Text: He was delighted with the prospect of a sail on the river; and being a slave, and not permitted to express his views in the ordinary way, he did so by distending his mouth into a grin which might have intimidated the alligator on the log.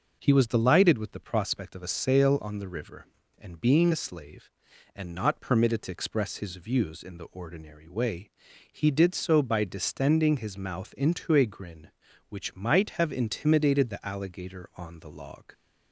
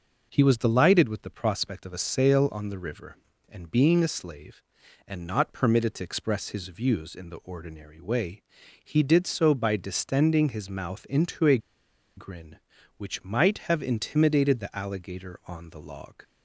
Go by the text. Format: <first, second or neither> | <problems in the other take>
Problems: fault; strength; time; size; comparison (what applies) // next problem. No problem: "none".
first | pauses between "a" and "grin"; noticeable; at 11.5 s; 0.58 s long